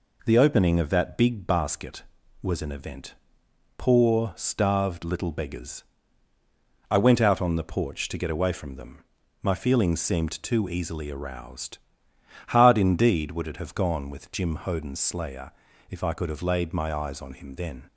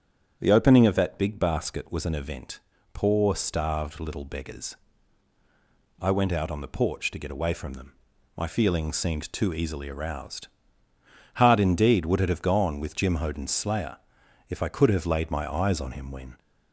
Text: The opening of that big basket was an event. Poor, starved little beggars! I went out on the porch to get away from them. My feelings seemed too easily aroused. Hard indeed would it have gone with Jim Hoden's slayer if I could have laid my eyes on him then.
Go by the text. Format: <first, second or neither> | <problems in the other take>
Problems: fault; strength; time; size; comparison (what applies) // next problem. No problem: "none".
first | starts louder than the rest; strong; until 1.4 s; 8.5 dB // pauses between "slayer" and "if"; noticeable; at 13.9 s; 0.52 s long; slight in the first // says "when" for "then"; at 16.1 s